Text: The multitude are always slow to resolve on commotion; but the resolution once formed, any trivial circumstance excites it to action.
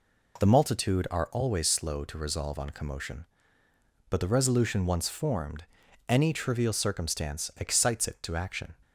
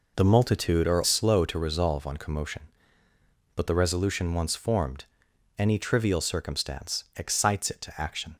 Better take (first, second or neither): first